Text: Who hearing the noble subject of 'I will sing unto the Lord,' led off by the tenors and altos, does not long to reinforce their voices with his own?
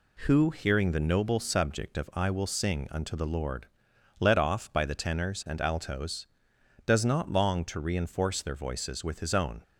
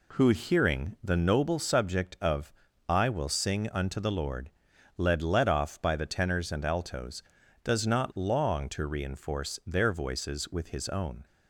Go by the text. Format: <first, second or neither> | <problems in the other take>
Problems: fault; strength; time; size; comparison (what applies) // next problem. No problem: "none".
first | pauses between "of" and "I"; at 2.5 s; 0.38 s long // says "led" twice; at 5.2 s